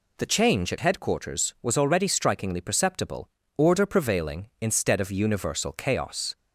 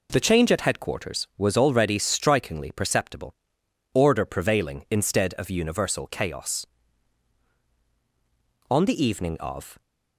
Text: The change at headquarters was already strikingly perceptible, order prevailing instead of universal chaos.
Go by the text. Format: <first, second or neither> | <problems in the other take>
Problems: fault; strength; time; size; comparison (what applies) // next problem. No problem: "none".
first | goes on to say "On the evening of"; noticeable; from 8.6 s on; 1.1 s long